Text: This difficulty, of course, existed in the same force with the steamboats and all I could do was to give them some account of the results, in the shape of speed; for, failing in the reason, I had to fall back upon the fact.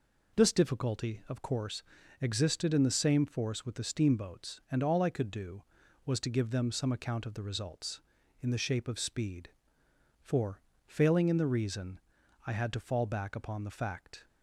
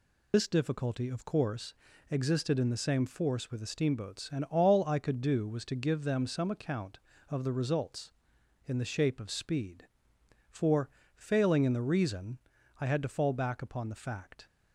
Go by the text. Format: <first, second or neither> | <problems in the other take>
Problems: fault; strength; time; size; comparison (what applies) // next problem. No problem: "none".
first | loses the start of "This"; at 0.3 s; 105 ms